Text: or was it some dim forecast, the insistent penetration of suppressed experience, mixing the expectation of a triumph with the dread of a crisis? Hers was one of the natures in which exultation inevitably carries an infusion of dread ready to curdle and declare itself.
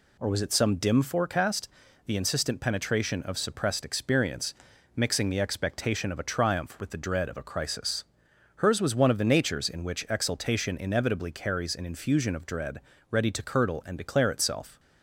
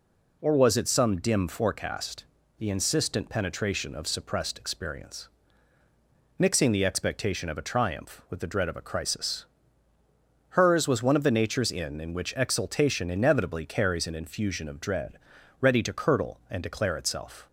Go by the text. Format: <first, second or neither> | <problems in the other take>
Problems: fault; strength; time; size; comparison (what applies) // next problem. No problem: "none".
first | says "in" twice; at 12.0 s // pauses between "dread" and "ready"; at 15.1 s; 0.42 s long; slight in the first